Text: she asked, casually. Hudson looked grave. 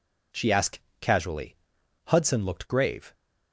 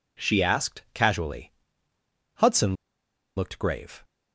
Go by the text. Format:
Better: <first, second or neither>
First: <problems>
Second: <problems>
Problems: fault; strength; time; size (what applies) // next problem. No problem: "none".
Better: first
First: none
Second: pauses between "Hudson" and "looked"; noticeable; at 2.7 s; 0.62 s long